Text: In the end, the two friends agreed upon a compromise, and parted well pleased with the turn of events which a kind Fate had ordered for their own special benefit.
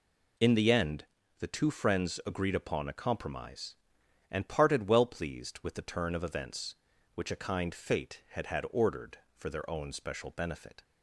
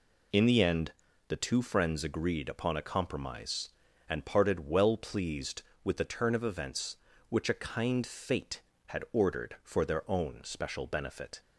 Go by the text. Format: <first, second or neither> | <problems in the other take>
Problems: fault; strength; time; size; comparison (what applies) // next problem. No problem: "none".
second | says "had" twice; at 8.4 s